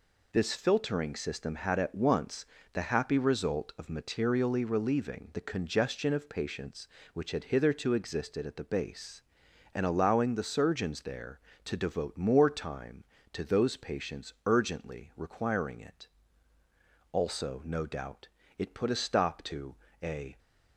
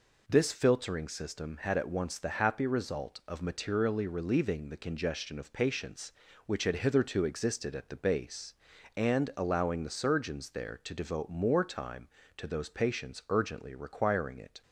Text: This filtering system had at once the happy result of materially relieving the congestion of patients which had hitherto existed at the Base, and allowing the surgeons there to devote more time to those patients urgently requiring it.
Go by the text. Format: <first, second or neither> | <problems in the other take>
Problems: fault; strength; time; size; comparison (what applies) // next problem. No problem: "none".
second | pauses between "once" and "the"; slight; at 2.4 s; 0.30 s long // goes on to say "Also no doubt it put a stop to a"; strong; from 17.1 s on; 3.2 s long